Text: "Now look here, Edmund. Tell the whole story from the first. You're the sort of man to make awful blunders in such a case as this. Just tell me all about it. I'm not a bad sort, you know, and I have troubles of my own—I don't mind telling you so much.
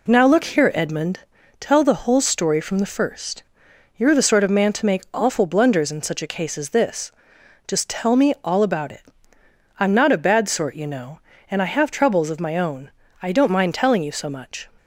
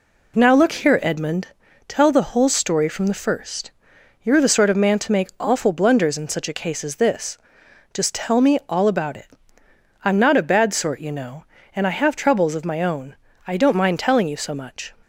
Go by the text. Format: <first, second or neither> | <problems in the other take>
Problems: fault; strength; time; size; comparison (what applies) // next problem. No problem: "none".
neither | none